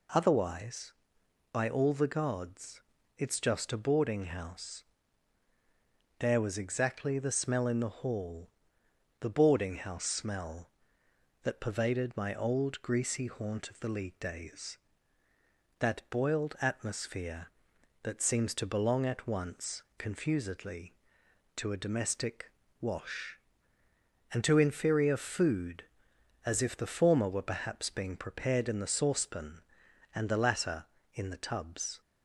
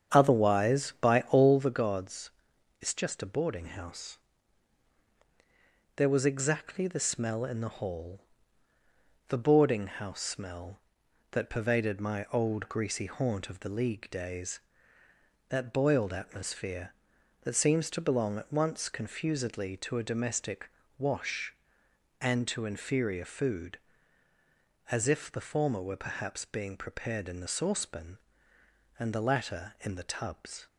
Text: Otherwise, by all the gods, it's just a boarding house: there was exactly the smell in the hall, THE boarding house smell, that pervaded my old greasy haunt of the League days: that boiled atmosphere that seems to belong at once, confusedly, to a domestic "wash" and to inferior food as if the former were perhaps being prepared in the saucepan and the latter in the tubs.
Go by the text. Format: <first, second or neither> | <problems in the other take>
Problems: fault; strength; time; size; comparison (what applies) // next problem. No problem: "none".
first | starts louder than the rest; strong; until 1.6 s; 8 dB // pauses between "domestic" and "wash"; slight; at 20.6 s; 0.30 s long; slight in the first